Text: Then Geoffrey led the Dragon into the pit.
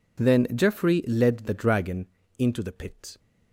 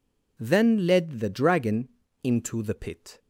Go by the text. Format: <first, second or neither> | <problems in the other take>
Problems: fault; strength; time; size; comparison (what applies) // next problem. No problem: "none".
first | skips "Geoffrey"; at 0.8 s // pauses between "Dragon" and "into"; slight; at 1.8 s; 0.34 s long; slight in the first